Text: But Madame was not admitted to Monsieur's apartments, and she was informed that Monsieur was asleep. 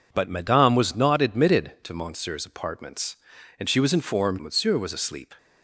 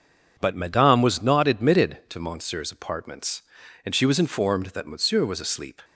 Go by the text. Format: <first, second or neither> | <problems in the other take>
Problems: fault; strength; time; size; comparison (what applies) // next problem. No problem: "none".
second | skips "that"; at 4.3 s